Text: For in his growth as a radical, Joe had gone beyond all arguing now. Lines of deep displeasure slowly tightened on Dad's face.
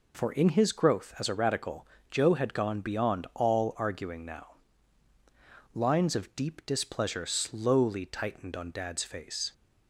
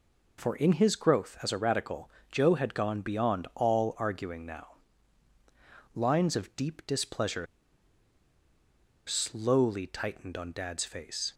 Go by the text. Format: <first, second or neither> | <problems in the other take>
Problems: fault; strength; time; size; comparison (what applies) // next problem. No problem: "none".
first | pauses between "displeasure" and "slowly"; strong; at 7.4 s; 1.6 s long